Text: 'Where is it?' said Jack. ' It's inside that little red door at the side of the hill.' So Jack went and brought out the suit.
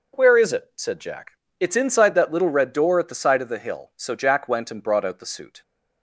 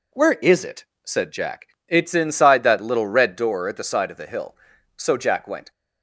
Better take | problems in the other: first | stops before "and brought out the suit"; at 5.7 s

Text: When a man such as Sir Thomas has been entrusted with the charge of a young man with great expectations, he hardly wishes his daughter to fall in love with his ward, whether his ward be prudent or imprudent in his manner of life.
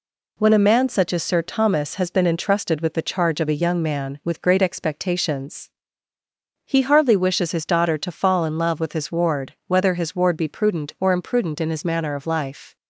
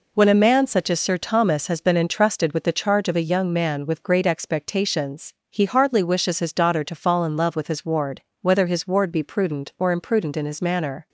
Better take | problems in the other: first | stops before "of life"; at 11.0 s

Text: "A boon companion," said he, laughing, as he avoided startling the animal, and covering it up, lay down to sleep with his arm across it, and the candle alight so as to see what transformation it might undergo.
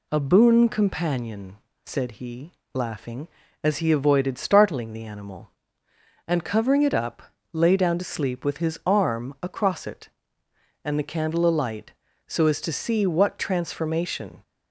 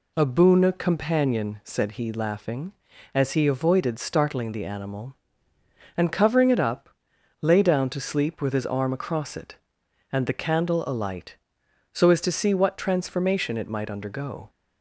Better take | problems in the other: second | stops before "it might undergo"; at 14.4 s

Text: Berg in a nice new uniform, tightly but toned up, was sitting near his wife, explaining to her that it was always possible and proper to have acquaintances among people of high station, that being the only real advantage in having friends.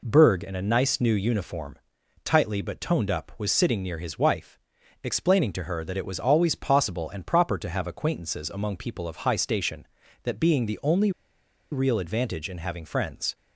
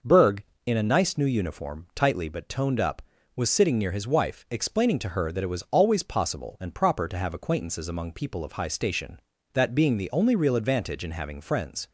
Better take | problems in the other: second | pauses between "only" and "real"; noticeable; at 11.0 s; 0.61 s long

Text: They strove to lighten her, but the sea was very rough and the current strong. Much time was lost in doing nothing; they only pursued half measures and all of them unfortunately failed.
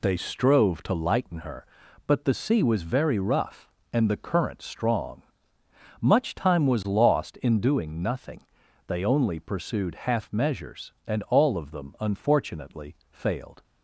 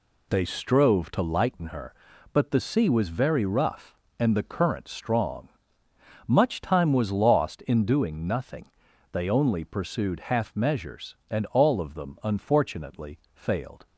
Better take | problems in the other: neither | pauses between "unfortunately" and "failed"; slight; the same in both

